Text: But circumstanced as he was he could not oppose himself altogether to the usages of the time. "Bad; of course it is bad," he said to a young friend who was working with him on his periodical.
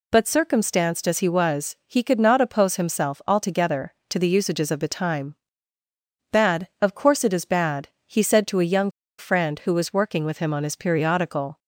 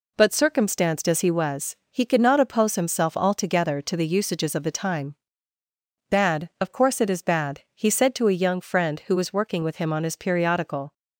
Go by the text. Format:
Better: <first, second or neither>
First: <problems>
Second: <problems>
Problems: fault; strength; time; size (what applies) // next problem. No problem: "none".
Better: second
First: pauses between "young" and "friend"; slight; at 8.8 s; 0.29 s long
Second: none